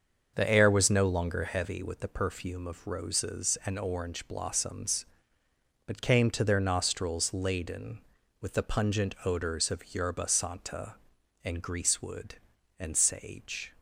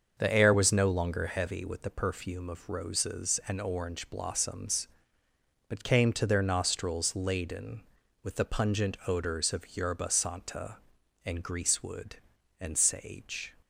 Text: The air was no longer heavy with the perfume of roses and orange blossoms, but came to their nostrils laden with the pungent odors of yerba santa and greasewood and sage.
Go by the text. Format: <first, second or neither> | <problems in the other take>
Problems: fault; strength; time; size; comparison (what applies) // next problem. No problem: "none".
neither | starts louder than the rest; the same in both